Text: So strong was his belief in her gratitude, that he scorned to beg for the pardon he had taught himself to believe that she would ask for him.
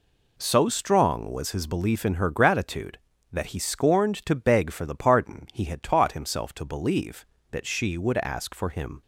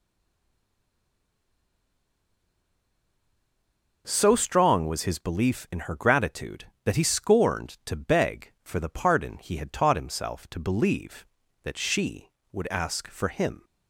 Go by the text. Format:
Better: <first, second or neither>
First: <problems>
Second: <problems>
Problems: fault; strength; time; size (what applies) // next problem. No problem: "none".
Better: first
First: none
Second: stays silent before the first word; strong; until 4.0 s; 4.0 s long